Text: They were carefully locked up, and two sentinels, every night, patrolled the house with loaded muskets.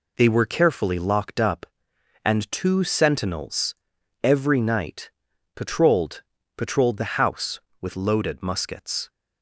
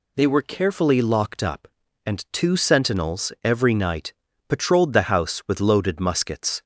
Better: second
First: says "patrolled" twice; at 6.5 s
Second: none

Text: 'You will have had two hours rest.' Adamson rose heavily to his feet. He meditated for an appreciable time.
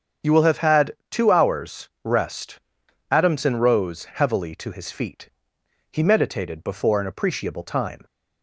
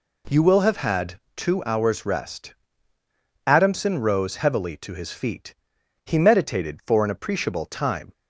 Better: second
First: starts louder than the rest; strong; until 1.4 s; 7.5 dB // pauses between "had" and "two"; slight; at 0.9 s; 0.16 s long // says "before" for "for"; at 6.6 s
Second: pauses between "had" and "two"; slight; at 1.1 s; 0.16 s long

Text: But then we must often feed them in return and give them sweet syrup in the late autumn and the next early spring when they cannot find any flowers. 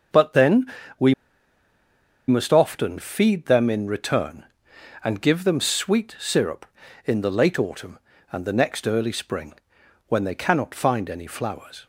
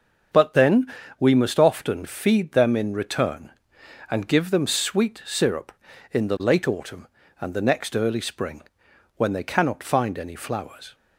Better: second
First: starts louder than the rest; until 2.5 s; 6 dB // pauses between "then" and "we"; slight; at 0.6 s; 0.32 s long // pauses between "we" and "must"; at 1.1 s; 1.1 s long // pauses between "spring" and "when"; noticeable; at 9.5 s; 0.54 s long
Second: starts louder than the rest; until 1.6 s; 6.5 dB // pauses between "then" and "we"; slight; at 0.8 s; 0.32 s long // pauses between "spring" and "when"; noticeable; at 8.6 s; 0.54 s long

